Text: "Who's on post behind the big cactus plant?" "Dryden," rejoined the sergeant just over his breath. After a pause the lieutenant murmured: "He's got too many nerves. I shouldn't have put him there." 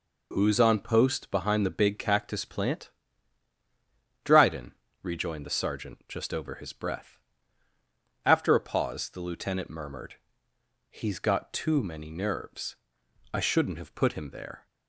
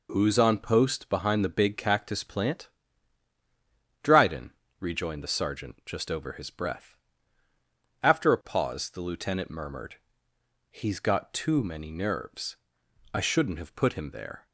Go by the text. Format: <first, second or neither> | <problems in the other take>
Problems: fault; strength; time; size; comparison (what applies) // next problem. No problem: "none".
neither | none